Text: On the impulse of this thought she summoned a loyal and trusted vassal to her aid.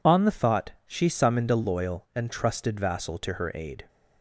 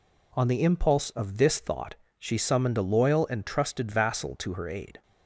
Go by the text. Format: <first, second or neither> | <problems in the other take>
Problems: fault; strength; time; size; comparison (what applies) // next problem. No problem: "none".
second | skips "impulse of this"; at 0.3 s // pauses between "thought" and "she"; slight; at 0.7 s; 0.16 s long; slight in the second